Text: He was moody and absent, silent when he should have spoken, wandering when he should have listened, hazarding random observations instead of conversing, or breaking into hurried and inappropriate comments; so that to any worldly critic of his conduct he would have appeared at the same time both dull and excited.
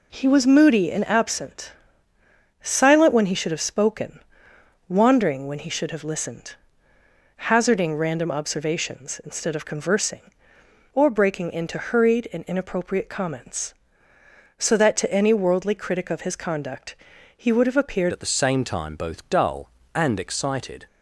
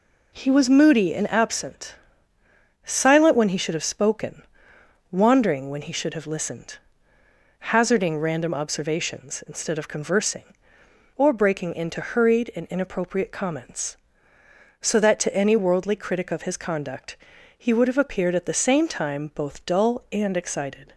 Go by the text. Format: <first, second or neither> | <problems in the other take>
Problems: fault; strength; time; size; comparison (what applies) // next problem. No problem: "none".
second | pauses between "conduct" and "he"; at 16.9 s; 0.40 s long; also in the second // changes voice at "at"; from 18.1 s on; 2.7 s long